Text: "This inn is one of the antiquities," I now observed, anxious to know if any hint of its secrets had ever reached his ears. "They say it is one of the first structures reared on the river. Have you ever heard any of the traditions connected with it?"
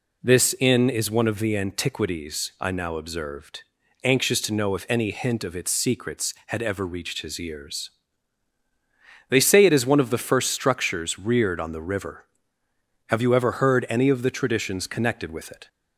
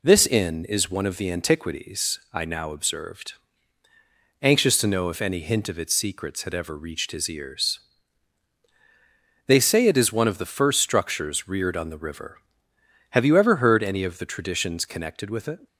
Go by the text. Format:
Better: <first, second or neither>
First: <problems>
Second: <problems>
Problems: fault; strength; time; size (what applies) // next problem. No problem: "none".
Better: neither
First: none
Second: none